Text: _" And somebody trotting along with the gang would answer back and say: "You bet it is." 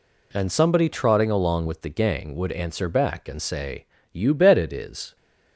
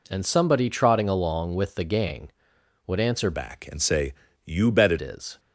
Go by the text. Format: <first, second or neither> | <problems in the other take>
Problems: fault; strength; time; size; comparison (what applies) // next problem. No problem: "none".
first | changes voice from "back" to "it"; from 3.3 to 4.9 s; 1.6 s long